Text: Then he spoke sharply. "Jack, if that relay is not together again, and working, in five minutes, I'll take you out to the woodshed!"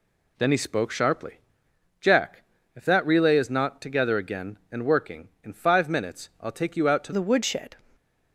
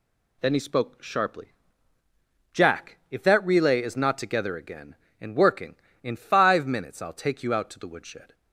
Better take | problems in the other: second | changes voice at "the"; from 7.1 s on; 0.6 s long

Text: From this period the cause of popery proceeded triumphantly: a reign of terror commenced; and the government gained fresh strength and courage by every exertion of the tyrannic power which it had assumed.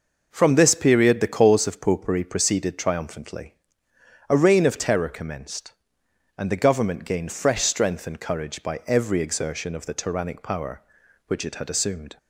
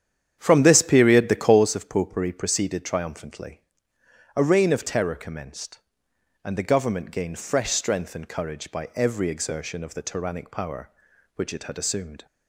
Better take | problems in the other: first | starts louder than the rest; strong; until 1.7 s; 9 dB

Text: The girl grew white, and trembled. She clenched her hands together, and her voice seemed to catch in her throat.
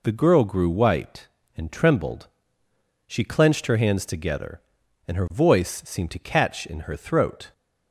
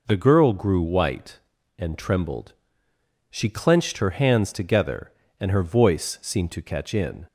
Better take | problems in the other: first | stops before "her throat"; at 7.2 s

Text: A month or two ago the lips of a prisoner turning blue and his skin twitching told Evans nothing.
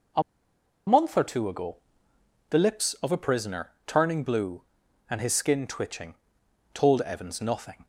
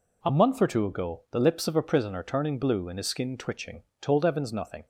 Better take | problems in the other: second | pauses between "A" and "month"; noticeable; at 0.2 s; 0.66 s long // pauses between "ago" and "the"; noticeable; at 1.7 s; 0.74 s long // pauses between "prisoner" and "turning"; slight; at 3.7 s; 0.16 s long // pauses between "twitching" and "told"; noticeable; at 6.1 s; 0.58 s long; slight in the second

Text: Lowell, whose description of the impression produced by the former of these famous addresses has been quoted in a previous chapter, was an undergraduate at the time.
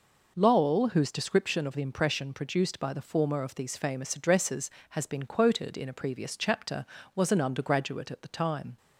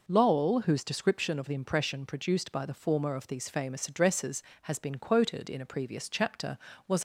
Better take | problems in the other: first | stops before "an undergraduate at the time"; at 6.9 s

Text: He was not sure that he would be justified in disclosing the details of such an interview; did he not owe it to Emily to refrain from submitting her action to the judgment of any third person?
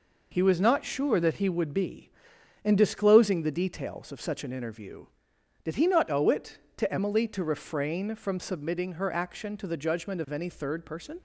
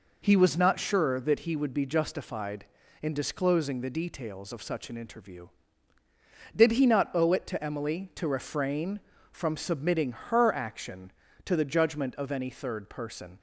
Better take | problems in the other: second | skips "justified"; at 2.3 s

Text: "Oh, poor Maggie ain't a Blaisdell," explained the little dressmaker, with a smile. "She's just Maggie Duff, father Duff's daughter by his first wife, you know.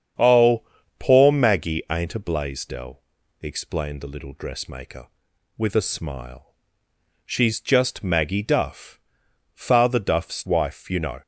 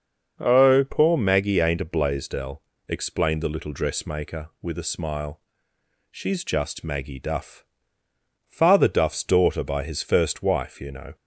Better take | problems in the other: second | starts louder than the rest; strong; until 1.5 s; 8 dB; noticeable in the second // skips "daughter by his first"; at 10.4 s

